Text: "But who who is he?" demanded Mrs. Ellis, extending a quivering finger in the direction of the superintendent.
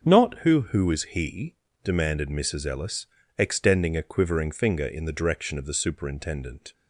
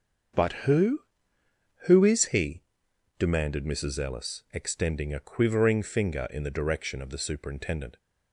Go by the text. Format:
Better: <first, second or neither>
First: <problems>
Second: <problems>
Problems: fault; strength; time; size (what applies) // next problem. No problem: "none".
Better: second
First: starts louder than the rest; until 1.0 s; 6.5 dB // says "Not" for "But"; at 0.0 s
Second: starts louder than the rest; strong; until 2.2 s; 7 dB